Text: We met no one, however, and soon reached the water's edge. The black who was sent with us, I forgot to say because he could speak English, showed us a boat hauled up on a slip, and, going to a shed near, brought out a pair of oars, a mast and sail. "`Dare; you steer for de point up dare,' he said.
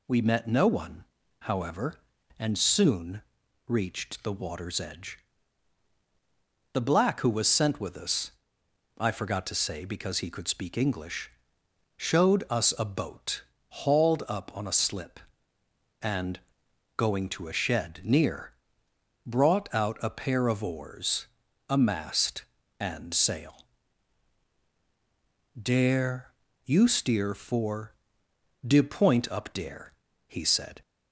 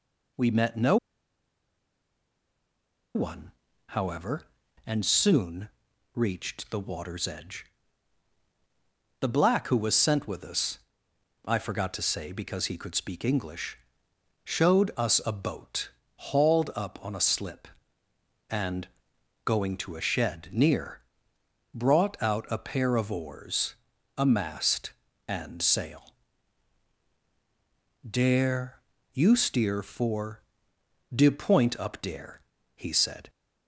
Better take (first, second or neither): first